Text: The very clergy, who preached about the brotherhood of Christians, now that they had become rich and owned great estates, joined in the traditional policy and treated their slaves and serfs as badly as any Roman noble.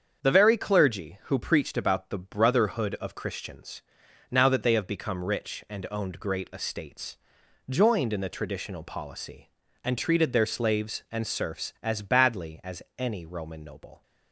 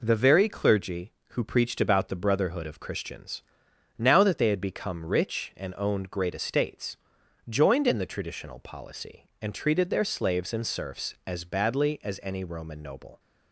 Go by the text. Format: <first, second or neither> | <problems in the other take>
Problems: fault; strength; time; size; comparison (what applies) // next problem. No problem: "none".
second | starts louder than the rest; strong; until 1.2 s; 7 dB // says "have" for "had"; at 4.7 s // pauses between "as" and "any"; slight; at 12.8 s; 0.16 s long